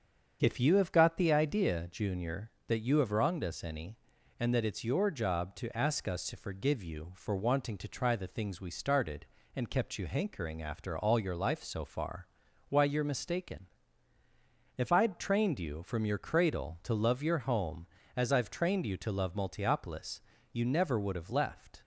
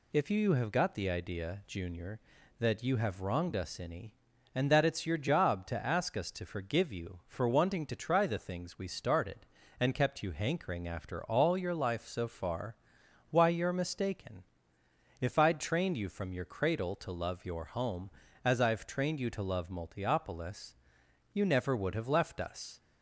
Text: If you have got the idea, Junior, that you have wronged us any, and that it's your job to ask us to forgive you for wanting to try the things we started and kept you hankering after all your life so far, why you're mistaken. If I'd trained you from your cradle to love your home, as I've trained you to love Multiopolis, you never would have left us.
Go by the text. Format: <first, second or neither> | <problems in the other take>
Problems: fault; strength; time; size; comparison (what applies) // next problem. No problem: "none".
second | starts louder than the rest; strong; until 1.4 s; 7 dB // stops before "us"; at 21.8 s